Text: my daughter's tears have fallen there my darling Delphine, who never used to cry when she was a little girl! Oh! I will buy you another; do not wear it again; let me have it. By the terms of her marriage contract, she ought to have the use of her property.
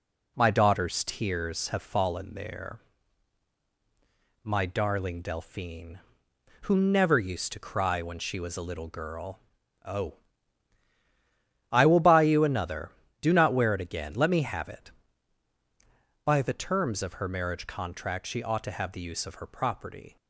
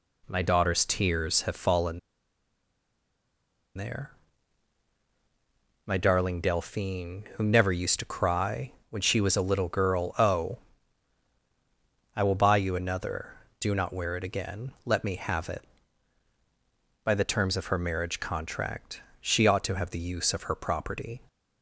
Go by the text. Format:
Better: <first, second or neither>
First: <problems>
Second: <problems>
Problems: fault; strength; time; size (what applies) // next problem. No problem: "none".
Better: first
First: pauses between "there" and "my"; strong; at 2.7 s; 1.6 s long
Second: pauses between "fallen" and "there"; strong; at 1.9 s; 1.7 s long // pauses between "there" and "my"; strong; at 4.1 s; 1.7 s long // pauses between "cry" and "when"; slight; at 8.7 s; 0.20 s long